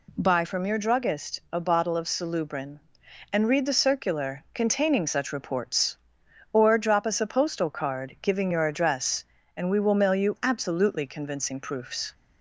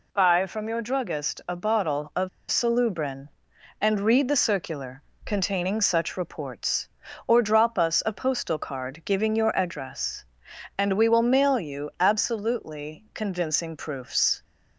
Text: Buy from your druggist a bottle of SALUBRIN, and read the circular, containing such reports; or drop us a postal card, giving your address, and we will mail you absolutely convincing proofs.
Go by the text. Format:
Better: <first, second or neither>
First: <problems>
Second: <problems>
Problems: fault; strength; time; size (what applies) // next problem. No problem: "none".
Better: first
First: none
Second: pauses between "of" and "SALUBRIN"; slight; at 2.2 s; 0.22 s long